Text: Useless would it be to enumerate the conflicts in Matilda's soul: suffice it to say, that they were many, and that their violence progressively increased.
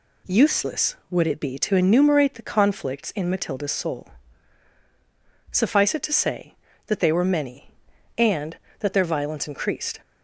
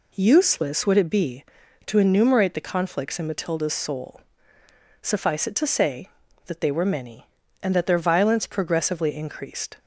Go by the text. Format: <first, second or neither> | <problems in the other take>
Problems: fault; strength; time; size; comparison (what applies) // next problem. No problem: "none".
second | skips "progressively"; at 9.4 s